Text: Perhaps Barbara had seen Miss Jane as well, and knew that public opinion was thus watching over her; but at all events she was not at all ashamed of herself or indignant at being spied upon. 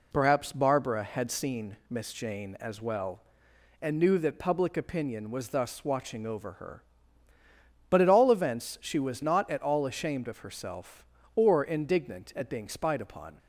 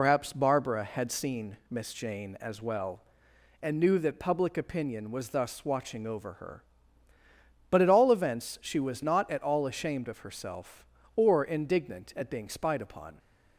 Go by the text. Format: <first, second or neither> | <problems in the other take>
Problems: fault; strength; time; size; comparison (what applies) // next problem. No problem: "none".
first | loses the start of "Perhaps"; at 0.0 s; 75 ms